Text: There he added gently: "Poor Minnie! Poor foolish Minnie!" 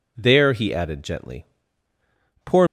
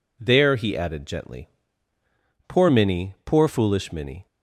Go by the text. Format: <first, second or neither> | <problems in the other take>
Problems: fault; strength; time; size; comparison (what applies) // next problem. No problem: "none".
second | stops before "Minnie Poor foolish Minnie"; at 2.6 s